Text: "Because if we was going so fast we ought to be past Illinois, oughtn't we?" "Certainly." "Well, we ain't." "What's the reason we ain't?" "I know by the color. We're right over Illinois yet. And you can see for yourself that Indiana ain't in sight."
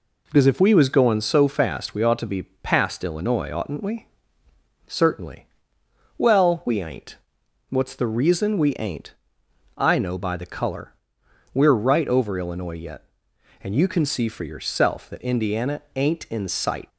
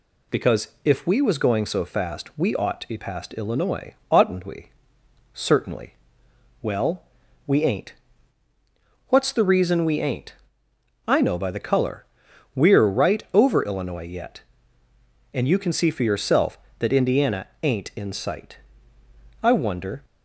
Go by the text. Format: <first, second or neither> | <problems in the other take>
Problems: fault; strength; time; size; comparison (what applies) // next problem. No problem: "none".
first | pauses between "Because" and "if"; slight; at 0.6 s; 0.16 s long // pauses between "Indiana" and "ain't"; slight; at 17.4 s; 0.16 s long // goes on to say "I wonder"; noticeable; from 19.4 s on; 0.62 s long